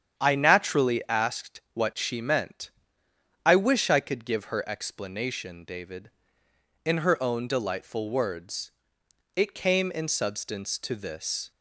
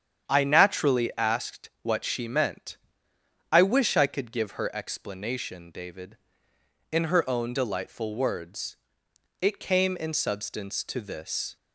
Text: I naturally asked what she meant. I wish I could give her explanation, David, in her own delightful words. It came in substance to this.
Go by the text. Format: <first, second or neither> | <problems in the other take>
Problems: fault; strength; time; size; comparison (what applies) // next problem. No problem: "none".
neither | starts louder than the rest; strong; the same in both